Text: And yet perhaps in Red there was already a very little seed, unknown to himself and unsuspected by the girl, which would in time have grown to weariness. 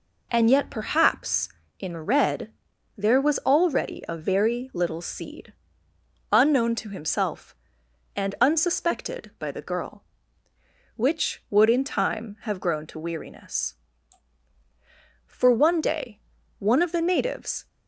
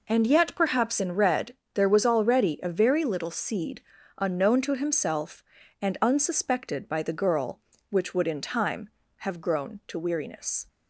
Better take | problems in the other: second | pauses between "Red" and "there"; noticeable; at 2.5 s; 0.46 s long; slight in the second // goes on to say "For one day one of the natives"; strong; from 15.2 s on; 2.4 s long

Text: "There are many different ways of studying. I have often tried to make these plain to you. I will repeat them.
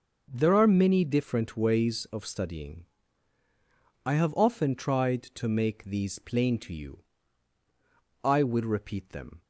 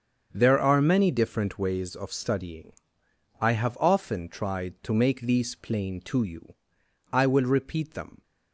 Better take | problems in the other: neither | starts louder than the rest; the same in both

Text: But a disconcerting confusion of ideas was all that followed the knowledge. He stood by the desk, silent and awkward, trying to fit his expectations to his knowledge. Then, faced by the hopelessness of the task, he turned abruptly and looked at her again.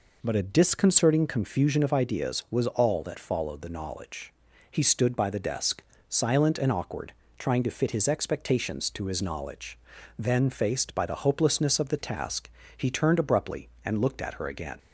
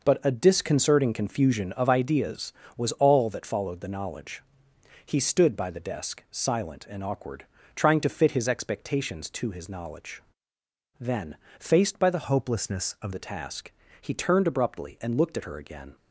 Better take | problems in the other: first | changes voice from "hopelessness" to "of"; from 12.2 to 13.1 s; 0.9 s long

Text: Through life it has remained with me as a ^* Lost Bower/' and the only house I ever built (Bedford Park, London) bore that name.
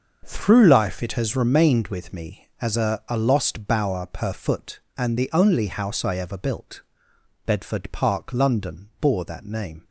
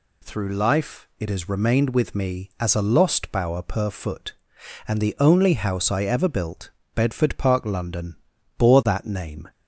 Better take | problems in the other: second | starts louder than the rest; until 1.2 s; 6 dB // says "a" twice; at 3.1 s

